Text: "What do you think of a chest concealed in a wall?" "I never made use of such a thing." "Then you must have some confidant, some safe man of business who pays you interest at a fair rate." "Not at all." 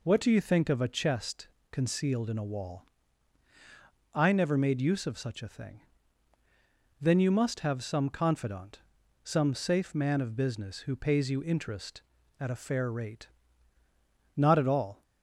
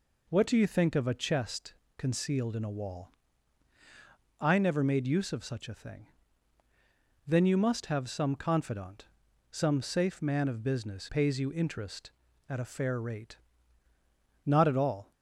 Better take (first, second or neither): first